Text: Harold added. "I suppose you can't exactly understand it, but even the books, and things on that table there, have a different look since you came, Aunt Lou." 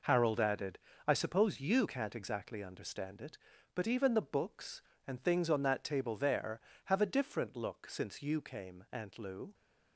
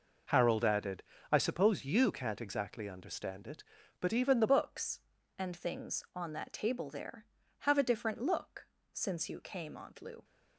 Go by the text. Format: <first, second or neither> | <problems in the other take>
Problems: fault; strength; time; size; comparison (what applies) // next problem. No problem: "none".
first | changes voice at "books"; from 4.4 s on; 5.8 s long // pauses between "look" and "since"; slight; at 8.6 s; 0.24 s long